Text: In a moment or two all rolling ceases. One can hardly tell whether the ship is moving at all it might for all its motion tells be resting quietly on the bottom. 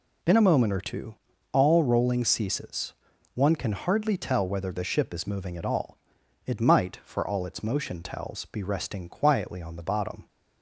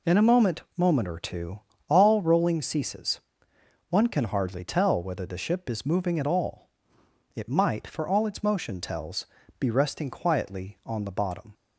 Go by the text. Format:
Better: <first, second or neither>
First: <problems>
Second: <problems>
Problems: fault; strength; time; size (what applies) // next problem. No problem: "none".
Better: first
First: pauses between "two" and "all"; slight; at 1.1 s; 0.36 s long // pauses between "all" and "it"; noticeable; at 5.9 s; 0.48 s long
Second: says "moment" twice; at 0.7 s // pauses between "two" and "all"; slight; at 1.6 s; 0.26 s long // pauses between "all" and "it"; noticeable; at 6.7 s; 0.64 s long // pauses between "tells" and "be"; slight; at 9.2 s; 0.32 s long